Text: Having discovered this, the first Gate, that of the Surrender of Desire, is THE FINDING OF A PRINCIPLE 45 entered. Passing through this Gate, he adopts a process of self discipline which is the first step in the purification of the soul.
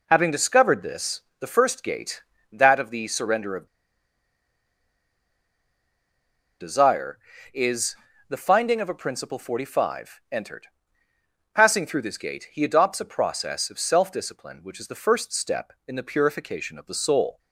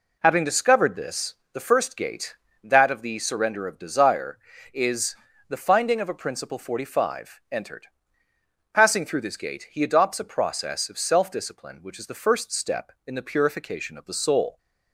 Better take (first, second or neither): second